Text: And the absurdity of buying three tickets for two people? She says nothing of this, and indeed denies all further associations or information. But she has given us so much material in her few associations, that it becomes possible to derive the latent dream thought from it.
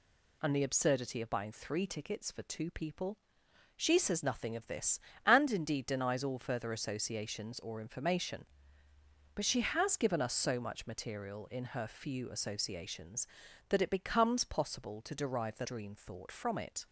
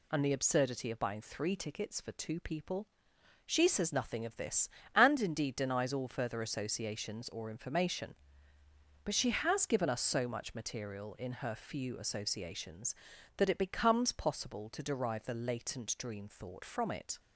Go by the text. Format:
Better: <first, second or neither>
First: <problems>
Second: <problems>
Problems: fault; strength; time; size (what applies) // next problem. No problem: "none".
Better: second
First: skips "latent"; at 15.6 s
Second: none